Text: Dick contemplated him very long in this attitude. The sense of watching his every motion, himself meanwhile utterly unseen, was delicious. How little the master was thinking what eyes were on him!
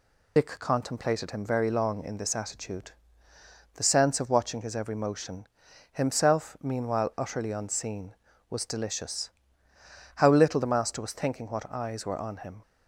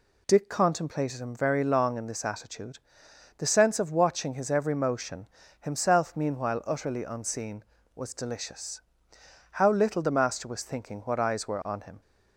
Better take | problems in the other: second | loses the start of "Dick"; at 0.3 s; 90 ms

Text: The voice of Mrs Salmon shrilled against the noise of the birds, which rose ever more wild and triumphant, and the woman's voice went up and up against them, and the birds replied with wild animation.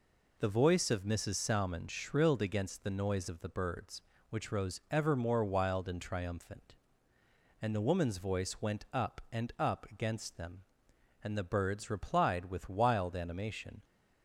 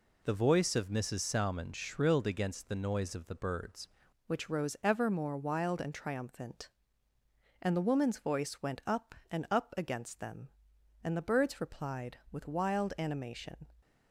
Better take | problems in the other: first | changes voice at "which"; from 4.2 s on; 9.4 s long

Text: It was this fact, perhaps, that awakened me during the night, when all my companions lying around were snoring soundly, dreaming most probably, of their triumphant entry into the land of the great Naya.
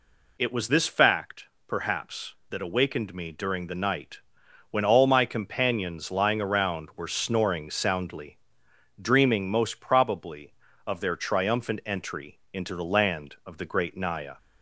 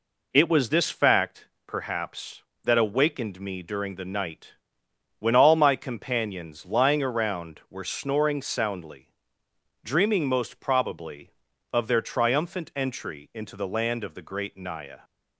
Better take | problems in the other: neither | none

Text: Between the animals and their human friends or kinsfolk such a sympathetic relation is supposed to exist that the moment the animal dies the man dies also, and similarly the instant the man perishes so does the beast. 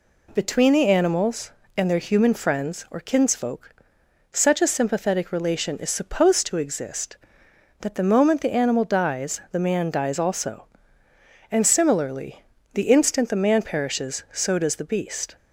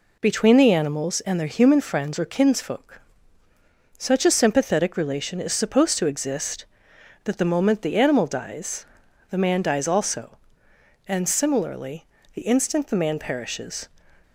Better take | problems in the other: first | pauses between "kinsfolk" and "such"; at 2.9 s; 1.0 s long; noticeable in the first // pauses between "dies" and "the"; noticeable; at 8.8 s; 0.46 s long // pauses between "similarly" and "the"; slight; at 12.0 s; 0.30 s long; slight in the first // stops before "so does the beast"; at 14.2 s

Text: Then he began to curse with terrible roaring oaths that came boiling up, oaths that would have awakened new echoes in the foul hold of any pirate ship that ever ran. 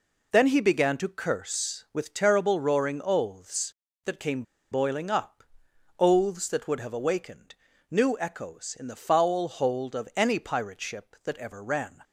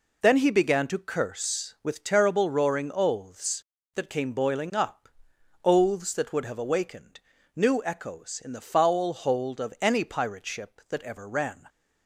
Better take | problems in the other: second | pauses between "came" and "boiling"; slight; at 4.4 s; 0.28 s long // pauses between "awakened" and "new"; slight; at 7.5 s; 0.34 s long; slight in the second

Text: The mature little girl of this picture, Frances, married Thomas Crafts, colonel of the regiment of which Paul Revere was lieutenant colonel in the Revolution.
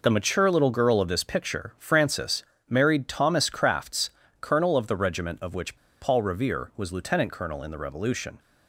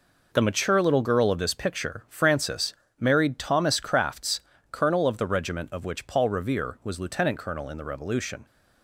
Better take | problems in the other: second | pauses between "which" and "Paul"; slight; at 5.7 s; 0.25 s long

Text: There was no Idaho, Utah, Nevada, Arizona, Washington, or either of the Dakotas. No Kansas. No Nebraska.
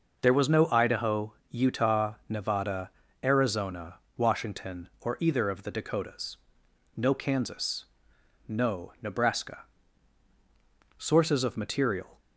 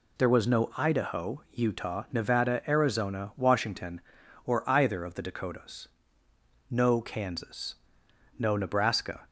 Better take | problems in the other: second | goes on to say "Sources of material"; noticeable; from 10.9 s on; 1.2 s long

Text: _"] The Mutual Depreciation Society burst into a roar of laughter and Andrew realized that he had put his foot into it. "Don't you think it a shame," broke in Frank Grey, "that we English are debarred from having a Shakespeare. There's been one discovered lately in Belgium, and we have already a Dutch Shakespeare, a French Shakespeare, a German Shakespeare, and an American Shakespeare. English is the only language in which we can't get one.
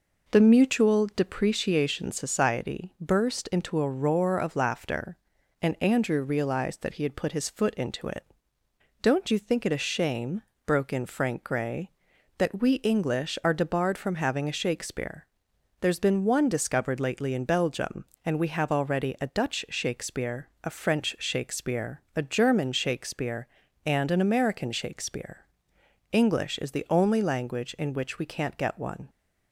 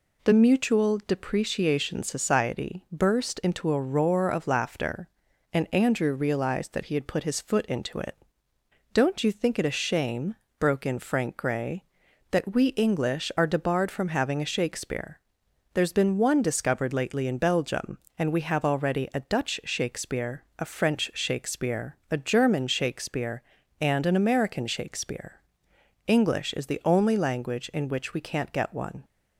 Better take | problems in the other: second | starts louder than the rest; noticeable; until 1.9 s; 5 dB

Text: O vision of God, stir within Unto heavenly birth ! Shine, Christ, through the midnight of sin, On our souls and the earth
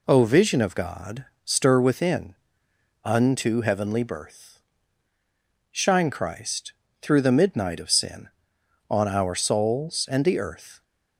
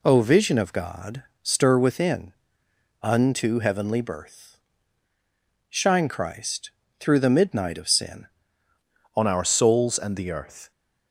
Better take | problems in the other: first | pauses between "within" and "Unto"; noticeable; at 2.3 s; 0.70 s long; noticeable in the first // changes voice at "On"; from 9.1 s on; 1.6 s long

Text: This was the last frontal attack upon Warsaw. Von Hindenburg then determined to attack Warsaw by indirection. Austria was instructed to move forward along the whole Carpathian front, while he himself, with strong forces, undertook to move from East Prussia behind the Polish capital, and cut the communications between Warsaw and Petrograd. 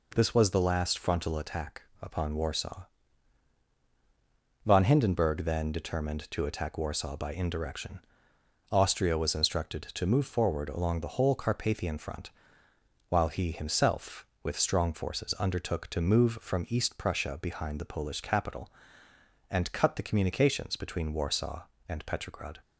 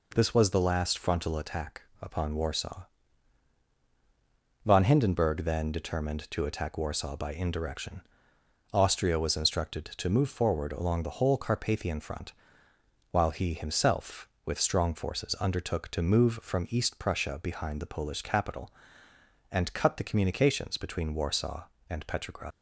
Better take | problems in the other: first | pauses between "attack" and "upon"; slight; at 1.8 s; 0.20 s long; slight in the first // leaves "Petrograd" unfinished; at 22.5 s; 115 ms

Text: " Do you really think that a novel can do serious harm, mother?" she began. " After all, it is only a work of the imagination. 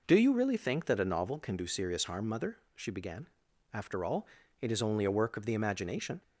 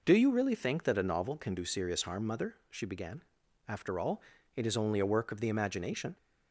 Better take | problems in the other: neither | none

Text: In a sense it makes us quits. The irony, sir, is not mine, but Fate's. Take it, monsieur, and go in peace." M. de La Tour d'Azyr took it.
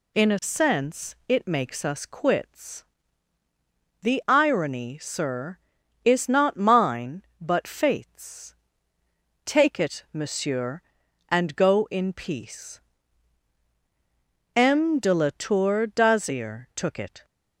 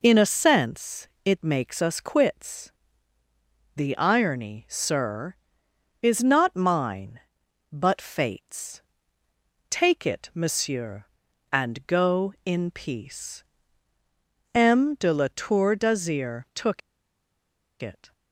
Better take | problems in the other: first | pauses between "sense" and "it"; slight; at 1.0 s; 0.18 s long // pauses between "took" and "it"; at 16.8 s; 1.0 s long

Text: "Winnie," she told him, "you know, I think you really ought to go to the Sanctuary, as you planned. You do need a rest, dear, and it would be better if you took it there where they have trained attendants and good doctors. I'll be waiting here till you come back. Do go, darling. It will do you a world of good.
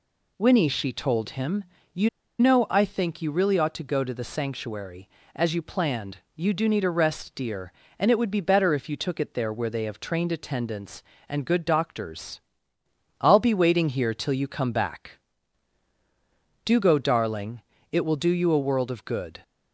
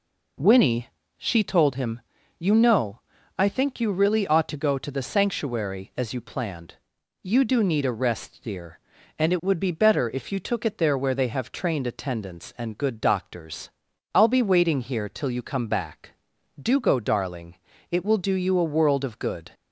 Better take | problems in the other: second | pauses between "you" and "know"; slight; at 2.0 s; 0.31 s long

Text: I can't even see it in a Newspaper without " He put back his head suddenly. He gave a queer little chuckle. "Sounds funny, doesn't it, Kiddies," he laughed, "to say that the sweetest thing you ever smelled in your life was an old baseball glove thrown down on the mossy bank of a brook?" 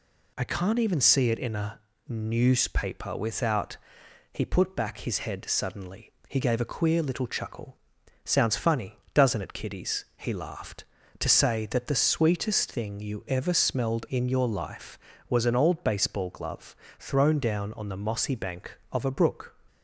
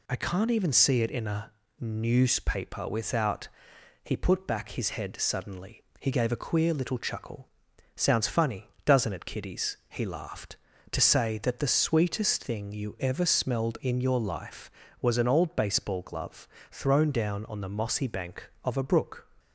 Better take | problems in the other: neither | pauses between "a" and "Newspaper"; slight; the same in both // pauses between "glove" and "thrown"; slight; the same in both

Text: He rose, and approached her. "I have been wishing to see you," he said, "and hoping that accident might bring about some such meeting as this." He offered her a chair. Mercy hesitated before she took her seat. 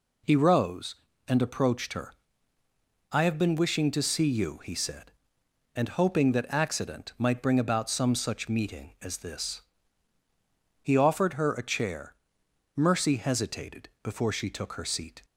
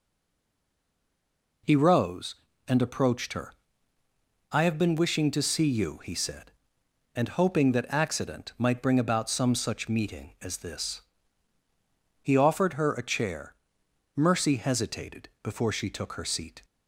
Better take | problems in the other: first | stays silent before the first word; noticeable; until 1.6 s; 1.6 s long

